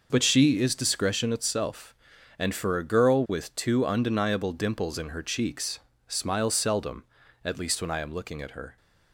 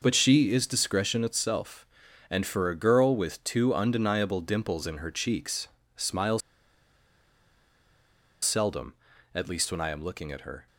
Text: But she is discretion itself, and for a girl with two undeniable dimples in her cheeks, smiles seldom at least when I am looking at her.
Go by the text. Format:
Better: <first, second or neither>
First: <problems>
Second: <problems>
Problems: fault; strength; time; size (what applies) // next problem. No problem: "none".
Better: first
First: none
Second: pauses between "smiles" and "seldom"; strong; at 6.4 s; 2.0 s long